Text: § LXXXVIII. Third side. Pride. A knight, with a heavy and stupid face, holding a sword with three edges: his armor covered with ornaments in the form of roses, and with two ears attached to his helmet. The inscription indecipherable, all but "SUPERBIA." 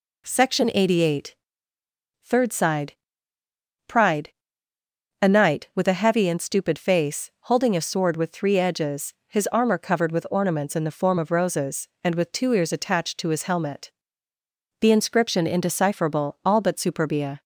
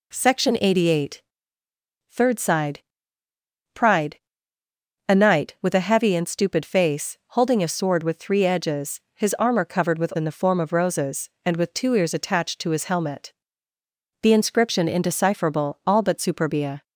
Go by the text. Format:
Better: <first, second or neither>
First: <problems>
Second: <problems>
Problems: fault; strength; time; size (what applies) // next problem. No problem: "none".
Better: first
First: none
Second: skips "ornaments"; at 10.1 s